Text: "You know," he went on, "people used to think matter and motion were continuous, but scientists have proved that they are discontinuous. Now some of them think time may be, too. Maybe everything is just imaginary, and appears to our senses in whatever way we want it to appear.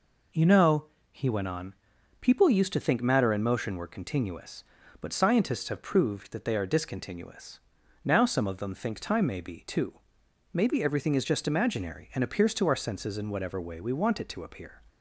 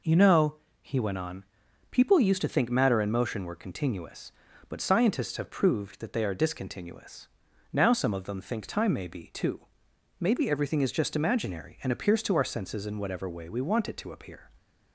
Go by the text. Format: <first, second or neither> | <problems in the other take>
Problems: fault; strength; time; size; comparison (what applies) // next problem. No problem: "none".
neither | none